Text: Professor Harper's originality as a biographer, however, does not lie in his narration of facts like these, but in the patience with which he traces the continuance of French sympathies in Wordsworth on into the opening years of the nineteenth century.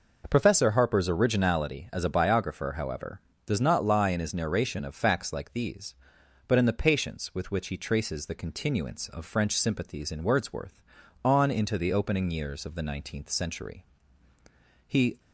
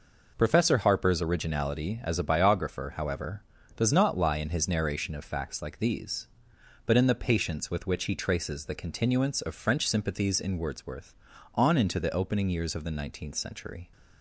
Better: second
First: goes on to say "He"; slight; from 14.8 s on; 0.32 s long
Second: none

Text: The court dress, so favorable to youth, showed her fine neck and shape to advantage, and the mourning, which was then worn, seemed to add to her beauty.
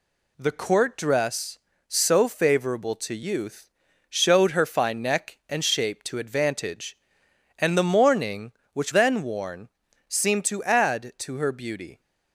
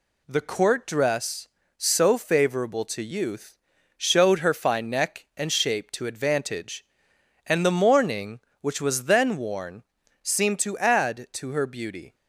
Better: second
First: skips "was"; at 8.9 s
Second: none

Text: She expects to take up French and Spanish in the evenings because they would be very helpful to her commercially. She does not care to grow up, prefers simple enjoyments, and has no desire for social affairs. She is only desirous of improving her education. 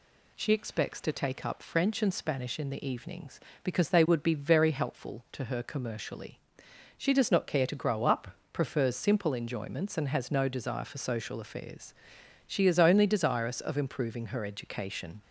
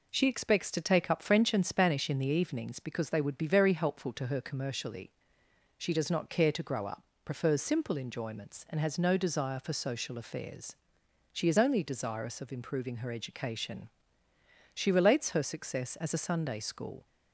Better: first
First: none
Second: goes on to say "She relates her success as a Sunday School"; strong; from 14.7 s on; 2.3 s long

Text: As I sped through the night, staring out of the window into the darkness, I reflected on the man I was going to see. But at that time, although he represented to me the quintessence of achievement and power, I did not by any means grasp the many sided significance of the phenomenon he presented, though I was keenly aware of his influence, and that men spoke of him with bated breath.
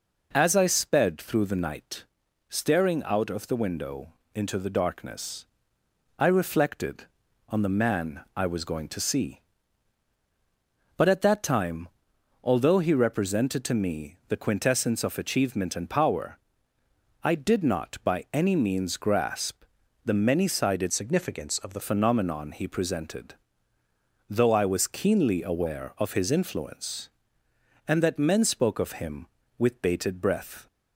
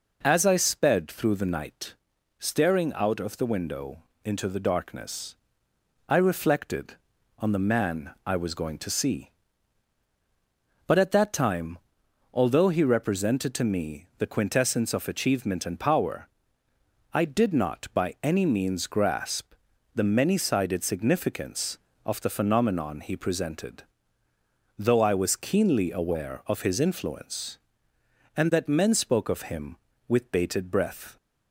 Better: second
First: pauses between "window" and "into"; slight; at 4.1 s; 0.20 s long // pauses between "grasp" and "the"; at 19.6 s; 0.42 s long // changes voice from "significance" to "the"; from 20.9 to 21.8 s; 0.9 s long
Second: pauses between "window" and "into"; slight; at 4.0 s; 0.20 s long // pauses between "grasp" and "the"; at 19.5 s; 0.42 s long

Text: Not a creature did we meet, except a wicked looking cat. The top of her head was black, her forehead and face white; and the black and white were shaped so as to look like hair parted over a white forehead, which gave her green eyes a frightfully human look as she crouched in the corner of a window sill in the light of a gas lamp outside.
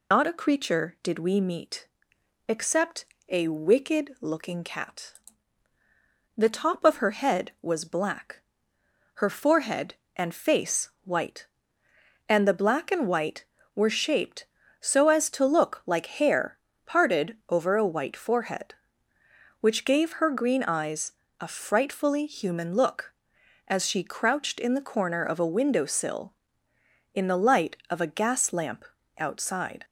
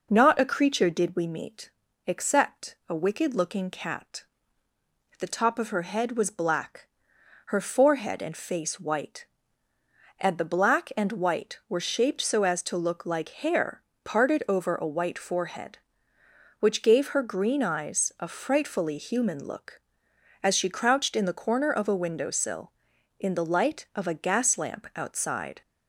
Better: second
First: loses the start of "Not"; at 0.1 s; 125 ms // pauses between "except" and "a"; slight; at 3.0 s; 0.24 s long // pauses between "face" and "white"; slight; at 10.8 s; 0.16 s long // pauses between "hair" and "parted"; slight; at 16.5 s; 0.28 s long // pauses between "eyes" and "a"; slight; at 21.1 s; 0.26 s long // pauses between "lamp" and "outside"; slight; at 28.8 s; 0.32 s long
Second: pauses between "hair" and "parted"; slight; at 13.8 s; 0.20 s long

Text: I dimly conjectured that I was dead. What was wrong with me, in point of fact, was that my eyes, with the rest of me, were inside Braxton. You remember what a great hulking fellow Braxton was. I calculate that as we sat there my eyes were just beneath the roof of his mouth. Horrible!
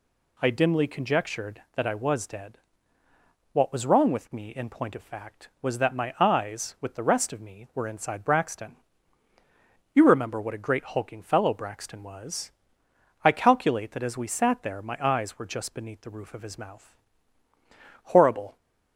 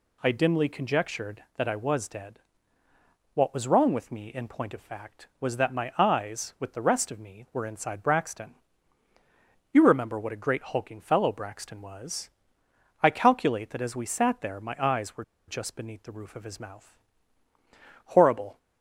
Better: first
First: none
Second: pauses between "were" and "just"; slight; at 15.2 s; 0.25 s long

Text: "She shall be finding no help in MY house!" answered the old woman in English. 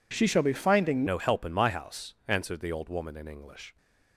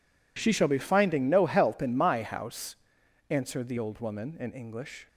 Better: second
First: changes voice at "no"; from 1.0 s on; 2.7 s long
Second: none

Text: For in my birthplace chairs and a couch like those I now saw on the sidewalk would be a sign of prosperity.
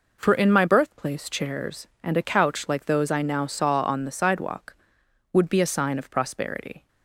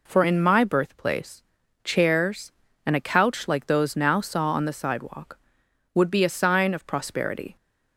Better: first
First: none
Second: pauses between "birthplace" and "chairs"; at 1.4 s; 0.42 s long // skips "I"; at 3.9 s

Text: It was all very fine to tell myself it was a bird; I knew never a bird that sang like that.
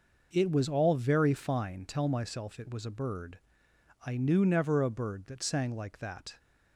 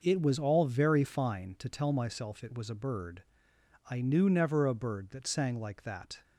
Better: second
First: skips "to"; at 1.8 s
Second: none

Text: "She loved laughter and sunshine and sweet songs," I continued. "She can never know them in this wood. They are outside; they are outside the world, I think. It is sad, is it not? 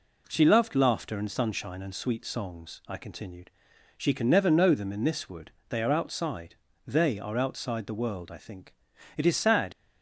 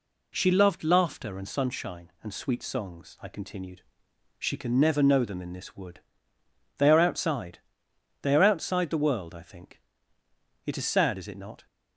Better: second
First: stops before "is it not"; at 9.7 s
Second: none

